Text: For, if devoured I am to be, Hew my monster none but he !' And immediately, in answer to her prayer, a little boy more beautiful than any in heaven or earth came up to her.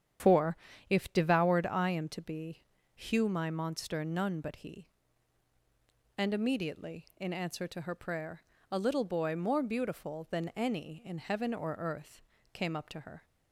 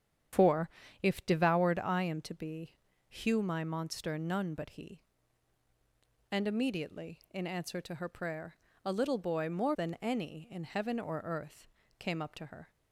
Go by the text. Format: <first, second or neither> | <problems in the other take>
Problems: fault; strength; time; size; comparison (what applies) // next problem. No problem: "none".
first | starts louder than the rest; strong; until 1.6 s; 9.5 dB; strong in the first // skips "beautiful"; at 9.7 s // pauses between "earth" and "came"; slight; at 11.6 s; 0.32 s long; slight in the first